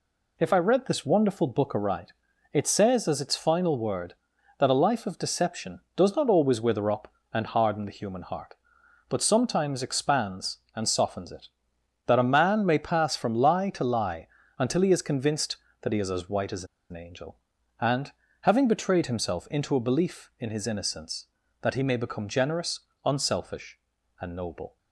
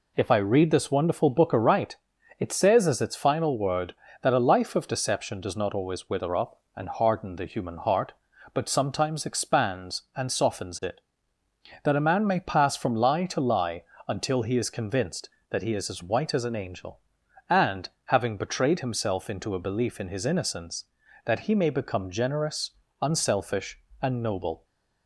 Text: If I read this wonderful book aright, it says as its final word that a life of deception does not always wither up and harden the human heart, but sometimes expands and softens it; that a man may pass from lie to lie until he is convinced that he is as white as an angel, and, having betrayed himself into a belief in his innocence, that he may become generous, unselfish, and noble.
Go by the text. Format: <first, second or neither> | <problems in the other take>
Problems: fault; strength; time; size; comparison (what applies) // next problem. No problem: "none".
second | pauses between "lie" and "until"; slight; at 14.2 s; 0.32 s long; slight in the second // pauses between "as" and "an"; slight; at 16.6 s; 0.25 s long